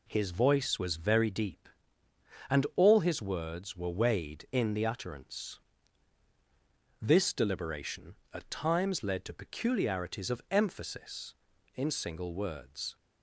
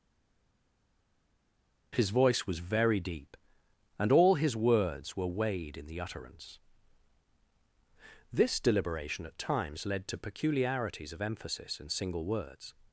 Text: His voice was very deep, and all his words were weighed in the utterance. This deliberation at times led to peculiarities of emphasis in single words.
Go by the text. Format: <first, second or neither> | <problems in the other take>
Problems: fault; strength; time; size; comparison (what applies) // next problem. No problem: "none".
first | stays silent before the first word; noticeable; until 1.9 s; 1.9 s long